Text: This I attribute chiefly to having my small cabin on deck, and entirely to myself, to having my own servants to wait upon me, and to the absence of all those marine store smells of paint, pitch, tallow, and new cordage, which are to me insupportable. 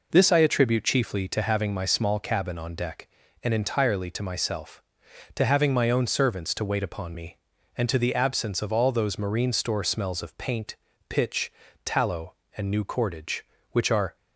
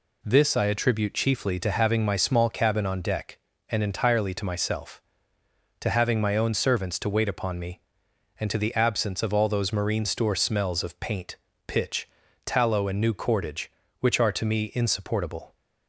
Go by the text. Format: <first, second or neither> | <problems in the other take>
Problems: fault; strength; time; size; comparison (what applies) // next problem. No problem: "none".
second | stops before "to me insupportable"; at 14.1 s